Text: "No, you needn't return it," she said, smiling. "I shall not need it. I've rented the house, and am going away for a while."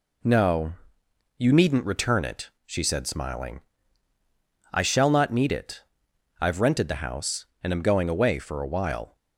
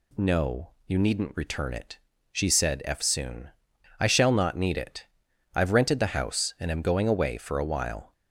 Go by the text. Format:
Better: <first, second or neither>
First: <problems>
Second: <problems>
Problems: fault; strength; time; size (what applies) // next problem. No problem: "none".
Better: first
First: none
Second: says "eftsoon" for "smiling"; at 2.8 s